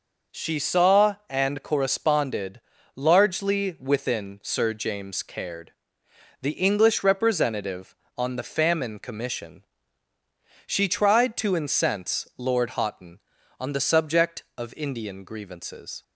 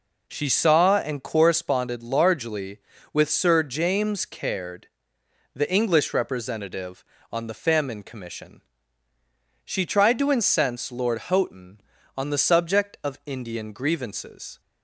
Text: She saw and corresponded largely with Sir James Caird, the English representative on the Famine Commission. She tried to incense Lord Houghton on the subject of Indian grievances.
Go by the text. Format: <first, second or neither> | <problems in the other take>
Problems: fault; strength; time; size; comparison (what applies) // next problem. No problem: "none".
second | pauses between "corresponded" and "largely"; slight; at 2.6 s; 0.34 s long // says "within" for "with"; at 3.7 s